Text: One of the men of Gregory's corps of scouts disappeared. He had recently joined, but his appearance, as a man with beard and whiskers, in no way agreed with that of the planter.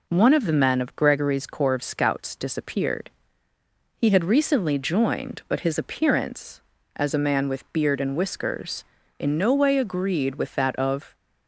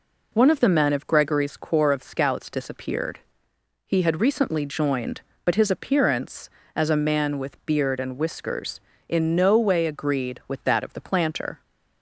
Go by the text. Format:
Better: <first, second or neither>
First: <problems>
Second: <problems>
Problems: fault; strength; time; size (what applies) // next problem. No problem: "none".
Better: second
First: stops before "the planter"; at 11.1 s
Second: none